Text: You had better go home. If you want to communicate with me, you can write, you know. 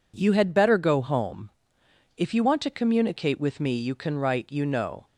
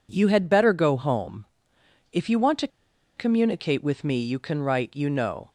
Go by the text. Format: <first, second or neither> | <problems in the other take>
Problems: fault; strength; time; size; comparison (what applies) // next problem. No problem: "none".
first | pauses between "to" and "communicate"; noticeable; at 2.6 s; 0.48 s long